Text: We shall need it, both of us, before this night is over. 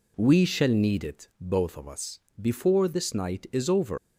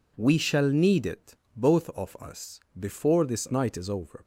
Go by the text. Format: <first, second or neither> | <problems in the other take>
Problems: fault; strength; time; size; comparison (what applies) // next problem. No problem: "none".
second | leaves "over" unfinished; at 3.9 s; 80 ms